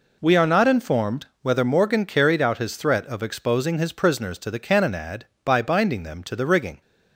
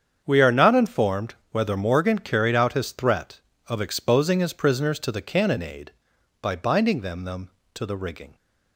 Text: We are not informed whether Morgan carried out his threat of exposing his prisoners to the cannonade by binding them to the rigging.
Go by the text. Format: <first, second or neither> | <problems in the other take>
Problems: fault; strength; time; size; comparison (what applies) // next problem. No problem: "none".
first | starts louder than the rest; strong; until 1.2 s; 7.5 dB // pauses between "informed" and "whether"; slight; at 1.3 s; 0.16 s long; slight in the first // says "them" twice; at 7.2 s